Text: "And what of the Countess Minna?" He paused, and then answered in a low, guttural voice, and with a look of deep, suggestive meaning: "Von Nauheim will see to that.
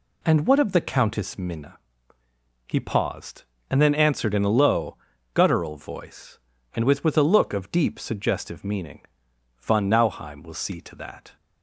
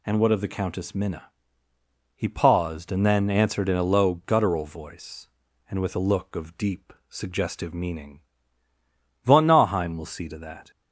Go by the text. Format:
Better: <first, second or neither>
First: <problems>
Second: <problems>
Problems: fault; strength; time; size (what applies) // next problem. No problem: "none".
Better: second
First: says "with" twice; at 7.0 s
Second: none